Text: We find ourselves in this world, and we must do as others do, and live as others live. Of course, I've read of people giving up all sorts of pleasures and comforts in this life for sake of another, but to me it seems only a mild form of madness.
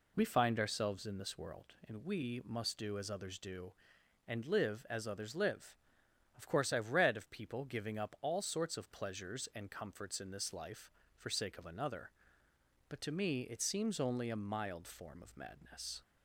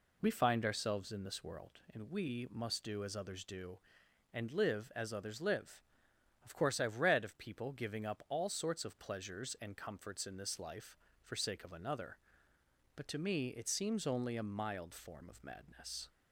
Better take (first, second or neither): neither